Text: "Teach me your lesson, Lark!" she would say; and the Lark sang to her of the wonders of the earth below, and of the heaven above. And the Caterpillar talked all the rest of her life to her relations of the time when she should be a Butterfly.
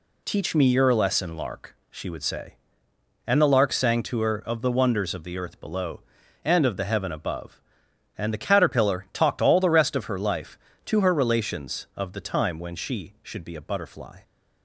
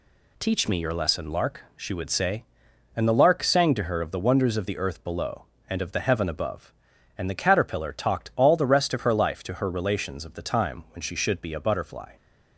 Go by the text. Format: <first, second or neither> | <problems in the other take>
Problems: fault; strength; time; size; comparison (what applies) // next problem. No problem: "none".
neither | none